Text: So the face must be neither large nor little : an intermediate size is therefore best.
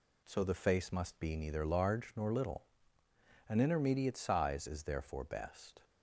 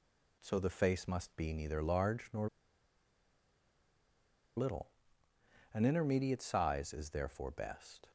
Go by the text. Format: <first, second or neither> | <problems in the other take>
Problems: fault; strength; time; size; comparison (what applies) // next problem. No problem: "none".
first | pauses between "nor" and "little"; strong; at 2.4 s; 2.0 s long